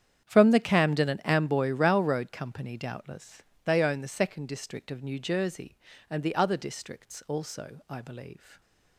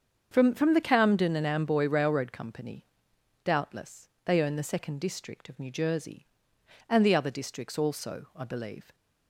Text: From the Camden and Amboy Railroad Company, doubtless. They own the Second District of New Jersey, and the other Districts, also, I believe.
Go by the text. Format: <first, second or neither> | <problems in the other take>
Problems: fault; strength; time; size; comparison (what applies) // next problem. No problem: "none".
first | starts louder than the rest; strong; until 1.3 s; 7 dB; strong in the first // says "From" twice; at 0.5 s